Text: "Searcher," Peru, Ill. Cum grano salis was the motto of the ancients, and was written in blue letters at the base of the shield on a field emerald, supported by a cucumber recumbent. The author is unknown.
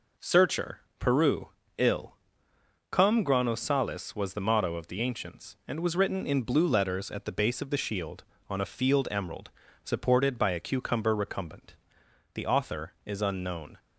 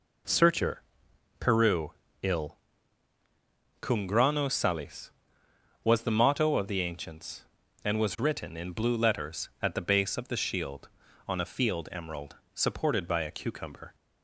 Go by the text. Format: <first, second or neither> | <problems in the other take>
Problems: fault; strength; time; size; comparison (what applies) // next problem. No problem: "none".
first | stops before "recumbent The author is unknown"; at 13.9 s